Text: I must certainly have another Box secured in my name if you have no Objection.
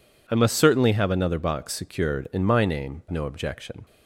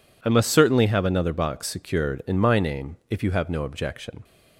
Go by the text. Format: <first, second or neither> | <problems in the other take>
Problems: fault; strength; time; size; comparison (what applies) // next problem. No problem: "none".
second | skips "if you have"; at 3.0 s